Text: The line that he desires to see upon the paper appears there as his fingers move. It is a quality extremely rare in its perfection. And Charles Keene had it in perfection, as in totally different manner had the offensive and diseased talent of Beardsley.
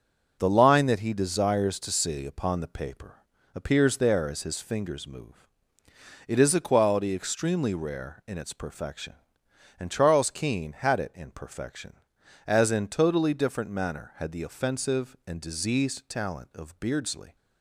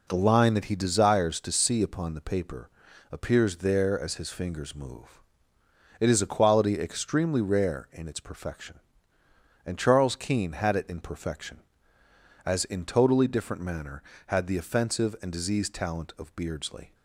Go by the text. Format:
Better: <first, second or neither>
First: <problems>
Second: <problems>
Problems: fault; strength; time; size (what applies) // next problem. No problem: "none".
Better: neither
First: pauses between "paper" and "appears"; slight; at 3.2 s; 0.32 s long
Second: pauses between "paper" and "appears"; at 2.6 s; 0.42 s long